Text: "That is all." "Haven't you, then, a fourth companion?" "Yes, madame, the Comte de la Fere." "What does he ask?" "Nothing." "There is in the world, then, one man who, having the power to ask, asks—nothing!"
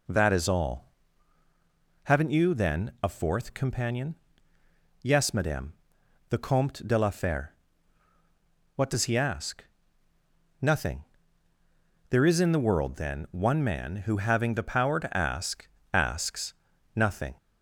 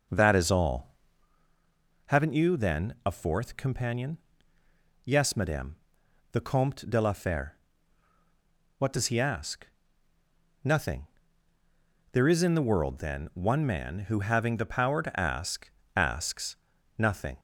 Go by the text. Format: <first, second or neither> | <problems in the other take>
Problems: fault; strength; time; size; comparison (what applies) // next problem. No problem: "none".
first | starts louder than the rest; noticeable; until 1.3 s; 6 dB